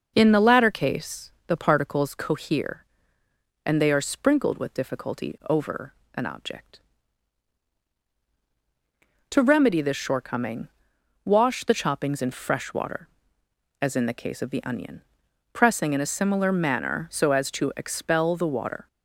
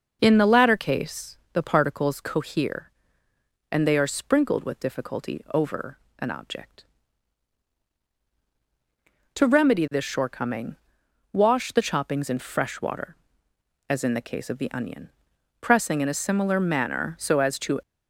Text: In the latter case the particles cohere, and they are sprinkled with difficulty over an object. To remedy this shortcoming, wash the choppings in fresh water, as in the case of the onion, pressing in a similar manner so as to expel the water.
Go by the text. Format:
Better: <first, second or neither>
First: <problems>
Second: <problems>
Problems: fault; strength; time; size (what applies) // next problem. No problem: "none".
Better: first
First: pauses between "case" and "the"; slight; at 1.3 s; 0.16 s long // pauses between "over" and "an"; slight; at 5.9 s; 0.22 s long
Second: pauses between "case" and "the"; slight; at 1.3 s; 0.16 s long // pauses between "over" and "an"; slight; at 5.9 s; 0.22 s long // stops before "expel the water"; at 17.8 s